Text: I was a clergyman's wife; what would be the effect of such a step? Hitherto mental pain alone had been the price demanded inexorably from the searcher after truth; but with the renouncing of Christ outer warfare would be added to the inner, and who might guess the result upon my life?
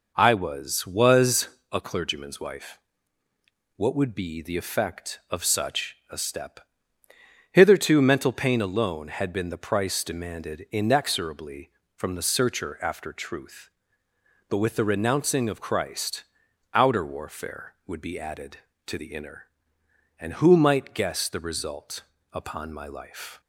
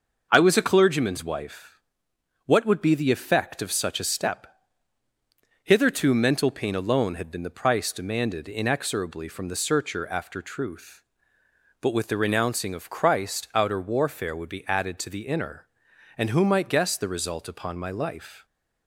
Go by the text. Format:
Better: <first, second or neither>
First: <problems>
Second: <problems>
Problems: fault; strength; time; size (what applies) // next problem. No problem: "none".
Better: second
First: says "was" twice; at 0.8 s // pauses between "Christ" and "outer"; noticeable; at 16.2 s; 0.50 s long // pauses between "result" and "upon"; slight; at 22.0 s; 0.32 s long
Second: none